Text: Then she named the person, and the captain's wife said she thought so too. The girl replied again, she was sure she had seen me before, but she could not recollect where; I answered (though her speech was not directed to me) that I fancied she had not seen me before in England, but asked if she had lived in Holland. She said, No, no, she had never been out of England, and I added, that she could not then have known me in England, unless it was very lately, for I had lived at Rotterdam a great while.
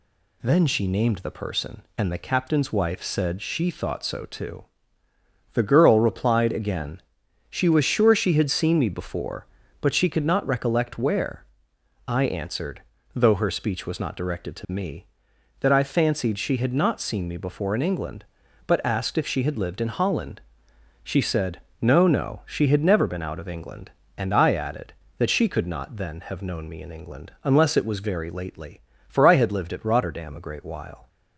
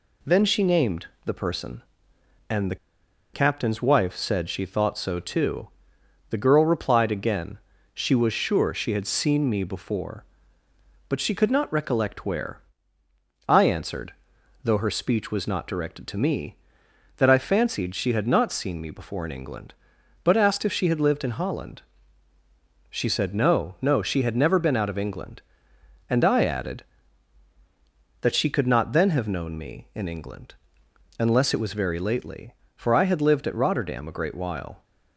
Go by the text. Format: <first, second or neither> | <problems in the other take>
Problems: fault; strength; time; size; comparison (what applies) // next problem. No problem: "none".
first | pauses between "named" and "the"; slight; at 1.0 s; 0.18 s long // pauses between "the" and "captain's"; noticeable; at 2.7 s; 0.57 s long